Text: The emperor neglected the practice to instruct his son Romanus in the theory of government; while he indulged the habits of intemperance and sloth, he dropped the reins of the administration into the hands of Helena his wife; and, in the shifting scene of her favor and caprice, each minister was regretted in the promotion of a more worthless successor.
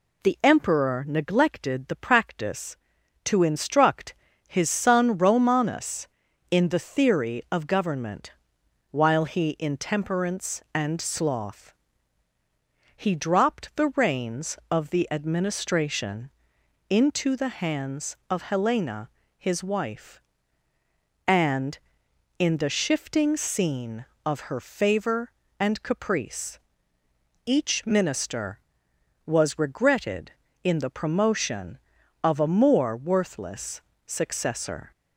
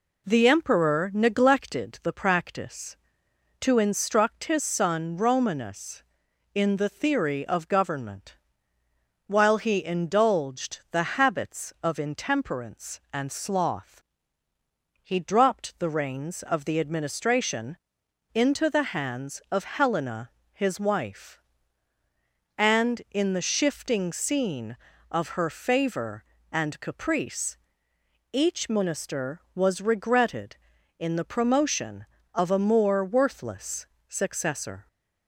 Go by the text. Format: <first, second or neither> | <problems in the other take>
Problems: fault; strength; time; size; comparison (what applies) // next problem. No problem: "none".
second | pauses between "instruct" and "his"; slight; at 4.1 s; 0.32 s long // skips "indulged the habits of"; at 9.5 s // pauses between "administration" and "into"; noticeable; at 16.3 s; 0.58 s long; noticeable in the second // pauses between "Helena" and "his"; slight; at 19.0 s; 0.28 s long; slight in the second // pauses between "worthless" and "successor"; slight; at 33.8 s; 0.24 s long; slight in the second